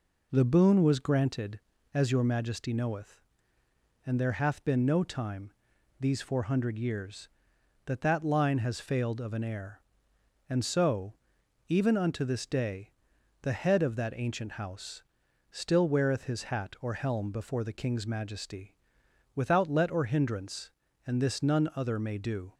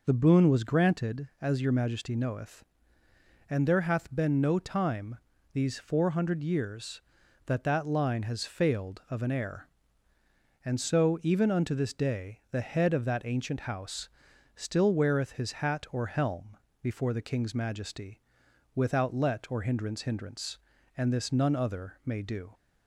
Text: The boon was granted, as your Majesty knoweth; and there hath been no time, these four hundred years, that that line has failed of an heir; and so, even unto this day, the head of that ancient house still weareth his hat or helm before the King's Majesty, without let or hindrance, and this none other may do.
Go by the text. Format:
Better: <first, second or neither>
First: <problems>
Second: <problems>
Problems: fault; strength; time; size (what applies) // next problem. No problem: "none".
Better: first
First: pauses between "house" and "still"; noticeable; at 15.0 s; 0.48 s long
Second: pauses between "house" and "still"; noticeable; at 14.0 s; 0.48 s long // pauses between "helm" and "before"; slight; at 16.5 s; 0.24 s long // says "hindrance" twice; at 20.0 s